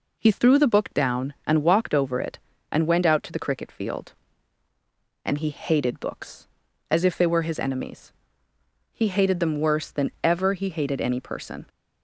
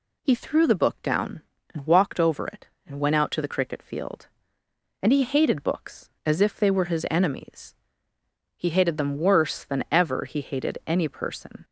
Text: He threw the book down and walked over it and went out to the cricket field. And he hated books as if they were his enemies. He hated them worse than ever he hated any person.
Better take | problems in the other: neither | none

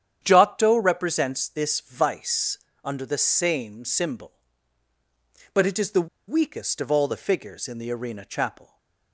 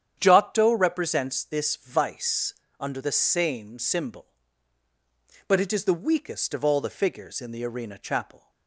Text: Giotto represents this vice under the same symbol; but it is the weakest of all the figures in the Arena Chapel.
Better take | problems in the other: second | starts louder than the rest; strong; until 1.2 s; 9 dB; strong in the second // pauses between "vice" and "under"; slight; at 2.5 s; 0.24 s long; slight in the second // pauses between "the" and "weakest"; slight; at 6.0 s; 0.20 s long

